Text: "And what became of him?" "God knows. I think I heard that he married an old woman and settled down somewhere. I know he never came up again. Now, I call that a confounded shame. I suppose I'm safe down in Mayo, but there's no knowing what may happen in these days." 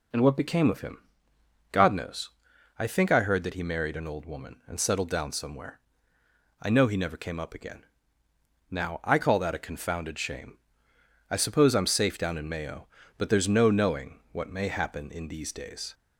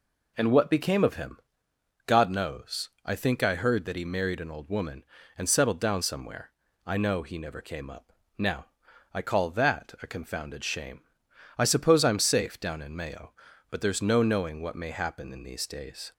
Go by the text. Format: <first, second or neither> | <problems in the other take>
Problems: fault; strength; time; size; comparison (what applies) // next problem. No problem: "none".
first | skips "again"; at 8.2 s